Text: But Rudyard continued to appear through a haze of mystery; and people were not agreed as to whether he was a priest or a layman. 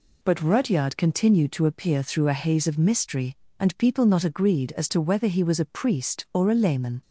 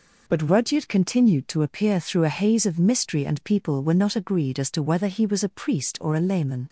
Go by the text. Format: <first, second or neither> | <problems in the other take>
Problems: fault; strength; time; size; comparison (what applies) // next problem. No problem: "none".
second | skips "were"; at 4.0 s